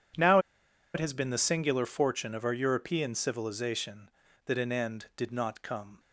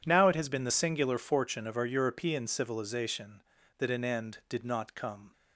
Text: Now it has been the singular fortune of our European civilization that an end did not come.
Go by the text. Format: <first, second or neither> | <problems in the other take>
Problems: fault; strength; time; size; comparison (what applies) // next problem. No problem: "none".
second | pauses between "Now" and "it"; noticeable; at 0.3 s; 0.55 s long